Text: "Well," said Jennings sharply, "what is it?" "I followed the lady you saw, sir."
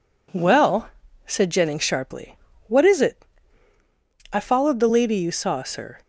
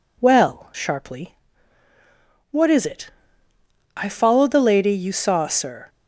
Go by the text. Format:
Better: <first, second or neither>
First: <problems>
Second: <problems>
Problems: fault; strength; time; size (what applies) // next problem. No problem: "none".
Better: first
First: none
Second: skips "said Jennings"; at 0.7 s